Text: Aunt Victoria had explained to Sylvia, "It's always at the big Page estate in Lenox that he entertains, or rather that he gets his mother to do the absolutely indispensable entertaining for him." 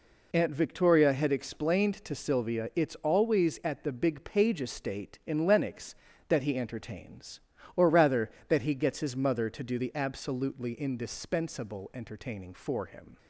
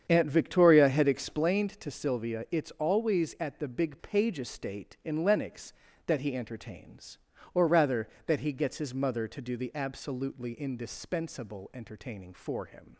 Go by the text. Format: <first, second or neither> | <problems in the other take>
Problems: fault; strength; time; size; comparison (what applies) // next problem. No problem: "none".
first | starts louder than the rest; strong; until 1.5 s; 8 dB